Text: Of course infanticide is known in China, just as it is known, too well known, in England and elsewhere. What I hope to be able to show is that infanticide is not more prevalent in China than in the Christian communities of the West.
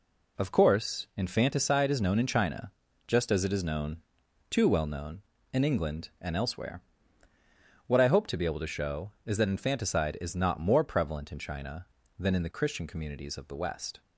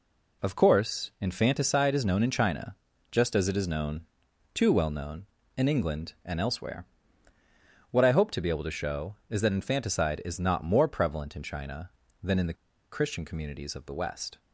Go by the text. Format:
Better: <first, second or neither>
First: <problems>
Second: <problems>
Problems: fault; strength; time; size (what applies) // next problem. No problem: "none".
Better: first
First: none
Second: pauses between "the" and "Christian"; at 12.5 s; 0.38 s long